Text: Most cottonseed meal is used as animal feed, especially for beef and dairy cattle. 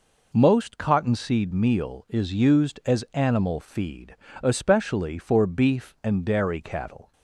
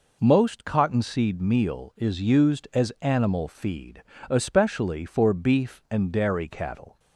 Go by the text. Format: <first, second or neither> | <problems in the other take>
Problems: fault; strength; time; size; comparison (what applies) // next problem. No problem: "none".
neither | none